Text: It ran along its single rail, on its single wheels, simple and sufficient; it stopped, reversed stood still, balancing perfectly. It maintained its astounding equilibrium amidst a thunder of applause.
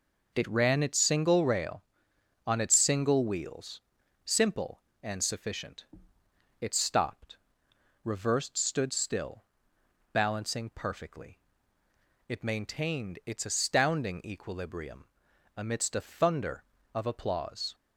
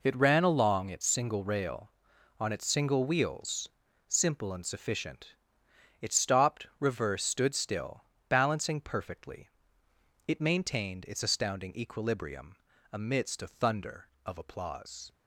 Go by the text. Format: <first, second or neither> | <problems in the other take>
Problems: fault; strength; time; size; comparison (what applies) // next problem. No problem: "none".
second | skips "along"; at 0.8 s // pauses between "equilibrium" and "amidst"; noticeable; at 15.0 s; 0.50 s long; slight in the second